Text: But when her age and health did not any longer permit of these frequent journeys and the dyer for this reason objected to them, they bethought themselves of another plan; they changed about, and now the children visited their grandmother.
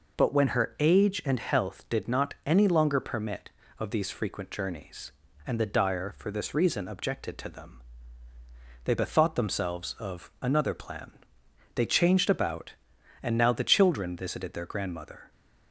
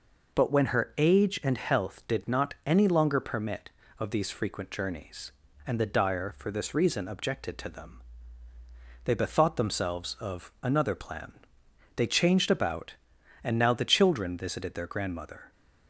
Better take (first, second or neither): neither